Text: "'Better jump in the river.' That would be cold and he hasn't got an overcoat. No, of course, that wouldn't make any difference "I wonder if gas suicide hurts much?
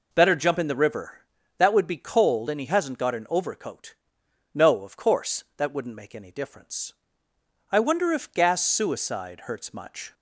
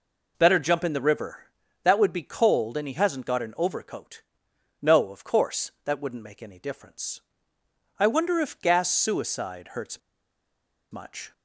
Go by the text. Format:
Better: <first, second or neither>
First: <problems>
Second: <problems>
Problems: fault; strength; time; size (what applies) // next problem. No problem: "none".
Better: first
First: pauses between "difference" and "I"; noticeable; at 6.9 s; 0.80 s long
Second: pauses between "difference" and "I"; noticeable; at 7.2 s; 0.80 s long // pauses between "hurts" and "much"; noticeable; at 9.9 s; 0.92 s long